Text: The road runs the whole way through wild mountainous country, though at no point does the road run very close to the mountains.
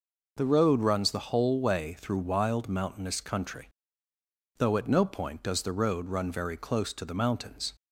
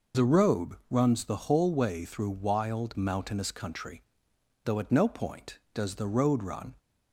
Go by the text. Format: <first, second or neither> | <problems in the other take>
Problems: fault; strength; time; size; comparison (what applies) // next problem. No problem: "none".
first | stops before "very close to the mountains"; at 6.7 s